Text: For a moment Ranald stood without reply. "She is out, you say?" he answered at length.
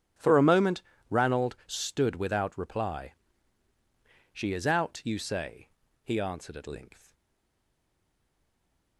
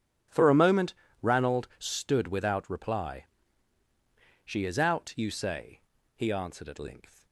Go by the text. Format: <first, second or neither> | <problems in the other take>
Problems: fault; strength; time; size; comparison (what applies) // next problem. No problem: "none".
second | pauses between "moment" and "Ranald"; slight; at 0.8 s; 0.30 s long; slight in the second // stays silent after the last word; noticeable; from 7.1 s on; 1.8 s long